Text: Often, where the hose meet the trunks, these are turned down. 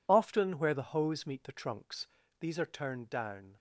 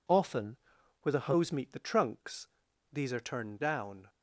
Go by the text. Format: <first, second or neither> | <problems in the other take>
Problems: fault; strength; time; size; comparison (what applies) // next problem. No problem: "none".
neither | none